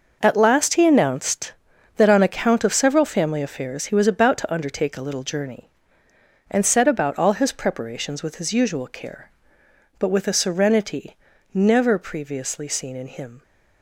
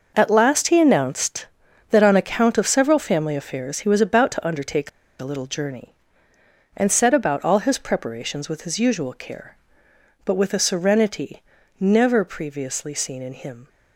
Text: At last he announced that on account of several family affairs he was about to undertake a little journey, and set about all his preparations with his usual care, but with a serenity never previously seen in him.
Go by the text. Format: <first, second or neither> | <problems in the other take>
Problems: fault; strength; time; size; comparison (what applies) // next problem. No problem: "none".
first | pauses between "undertake" and "a"; slight; at 4.8 s; 0.30 s long // pauses between "serenity" and "never"; slight; at 11.4 s; 0.36 s long; slight in the first